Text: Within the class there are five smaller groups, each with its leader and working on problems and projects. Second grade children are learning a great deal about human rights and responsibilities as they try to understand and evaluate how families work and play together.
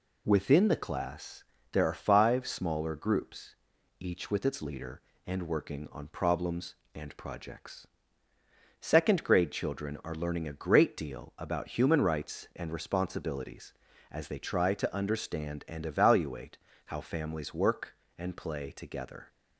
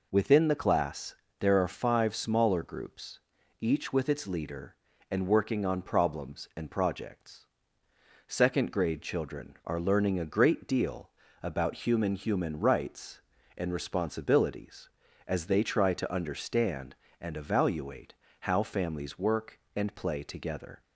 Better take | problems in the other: first | pauses between "class" and "there"; slight; at 1.1 s; 0.24 s long; slight in the first // pauses between "deal" and "about"; slight; at 11.1 s; 0.32 s long // says "human" twice; at 12.1 s // pauses between "evaluate" and "how"; slight; at 18.1 s; 0.26 s long; slight in the first

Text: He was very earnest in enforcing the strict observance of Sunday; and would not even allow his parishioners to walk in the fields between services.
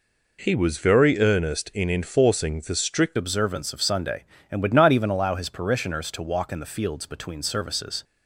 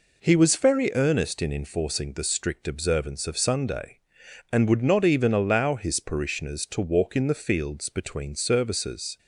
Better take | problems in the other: second | changes voice at "observance"; from 3.1 s on; 4.9 s long

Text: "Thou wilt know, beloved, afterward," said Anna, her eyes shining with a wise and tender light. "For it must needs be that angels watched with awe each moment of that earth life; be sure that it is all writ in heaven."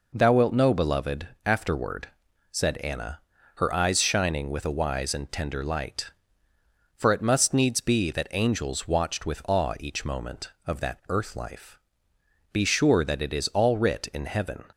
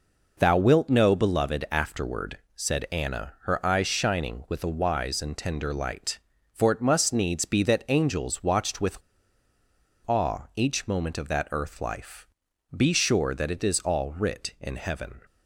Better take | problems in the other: first | pauses between "with" and "awe"; at 8.9 s; 1.0 s long

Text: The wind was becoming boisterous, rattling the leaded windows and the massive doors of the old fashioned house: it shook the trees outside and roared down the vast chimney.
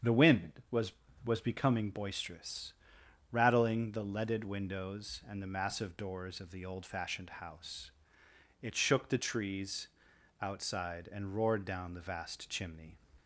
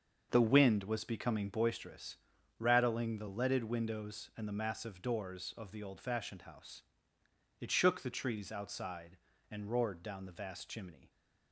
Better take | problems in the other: second | starts louder than the rest; strong; until 1.5 s; 7.5 dB; also in the second // says "was" twice; at 1.2 s // pauses between "trees" and "outside"; noticeable; at 9.8 s; 0.52 s long

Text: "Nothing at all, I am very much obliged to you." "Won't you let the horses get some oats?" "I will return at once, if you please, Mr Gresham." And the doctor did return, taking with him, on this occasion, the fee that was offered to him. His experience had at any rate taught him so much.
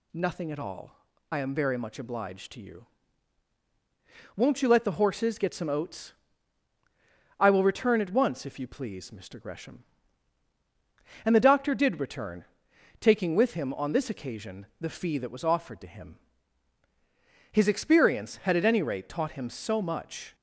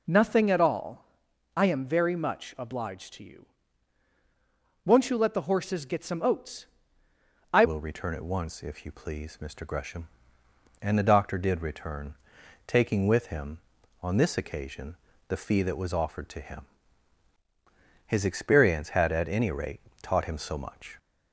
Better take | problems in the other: first | changes voice at "will"; from 7.6 s on; 13.3 s long // pauses between "rate" and "taught"; slight; at 19.7 s; 0.22 s long

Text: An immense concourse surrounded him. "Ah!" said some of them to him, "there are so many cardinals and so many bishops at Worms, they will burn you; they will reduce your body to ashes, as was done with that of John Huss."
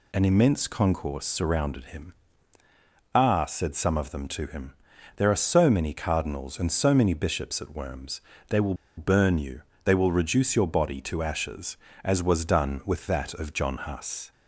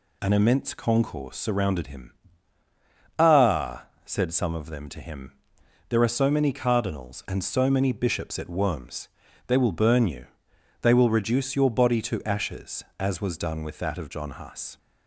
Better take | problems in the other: second | pauses between "will" and "burn"; slight; at 8.7 s; 0.23 s long

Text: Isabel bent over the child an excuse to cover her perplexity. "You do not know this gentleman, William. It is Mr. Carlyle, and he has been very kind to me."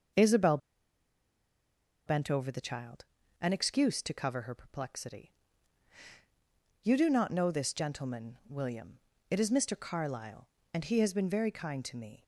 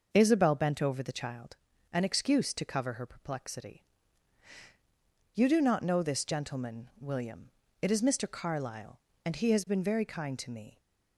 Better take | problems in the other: second | pauses between "Isabel" and "bent"; strong; at 0.5 s; 1.4 s long // pauses between "child" and "an"; at 3.0 s; 0.38 s long; also in the second

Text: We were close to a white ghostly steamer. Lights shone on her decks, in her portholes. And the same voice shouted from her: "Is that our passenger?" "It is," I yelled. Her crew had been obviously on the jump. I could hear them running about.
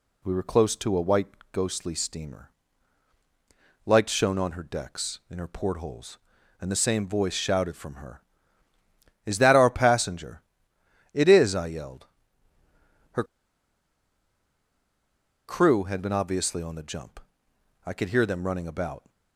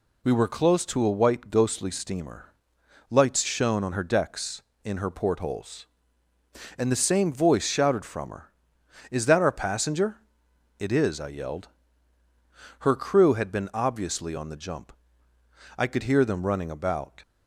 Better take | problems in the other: second | pauses between "white" and "ghostly"; slight; at 1.2 s; 0.24 s long // pauses between "Her" and "crew"; strong; at 13.2 s; 2.2 s long

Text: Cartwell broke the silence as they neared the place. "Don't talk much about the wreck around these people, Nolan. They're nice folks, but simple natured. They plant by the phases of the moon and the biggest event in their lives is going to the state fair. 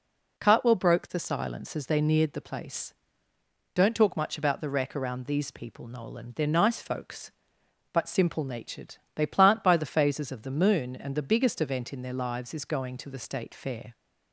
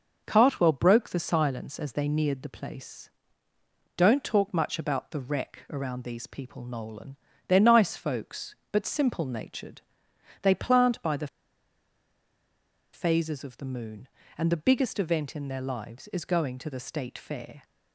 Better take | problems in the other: first | starts louder than the rest; noticeable; until 1.2 s; 6 dB // pauses between "the" and "phases"; strong; at 11.2 s; 1.6 s long

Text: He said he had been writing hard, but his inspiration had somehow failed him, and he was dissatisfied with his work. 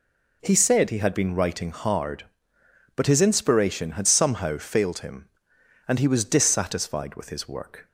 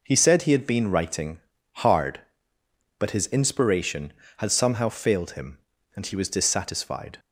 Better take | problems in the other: first | pauses between "writing" and "hard"; at 1.3 s; 0.38 s long // stops before "with his work"; at 7.1 s

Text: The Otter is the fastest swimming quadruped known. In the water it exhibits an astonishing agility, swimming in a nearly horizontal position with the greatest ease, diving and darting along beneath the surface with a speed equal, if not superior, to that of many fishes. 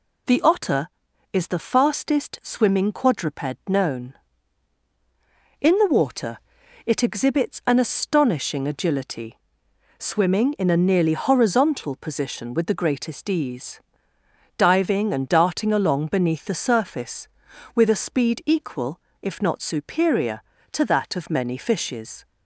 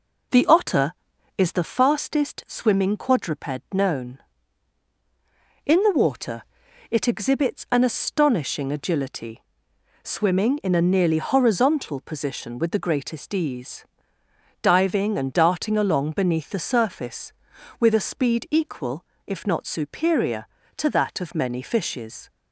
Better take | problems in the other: first | starts louder than the rest; noticeable; until 1.8 s; 4.5 dB // pauses between "water" and "it"; noticeable; at 6.4 s; 0.48 s long; noticeable in the first

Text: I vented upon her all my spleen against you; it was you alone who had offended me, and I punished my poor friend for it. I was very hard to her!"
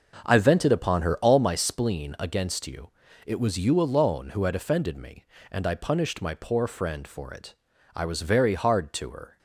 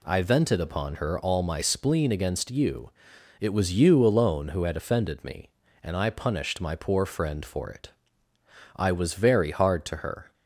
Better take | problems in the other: second | starts louder than the rest; noticeable; until 1.5 s; 6 dB

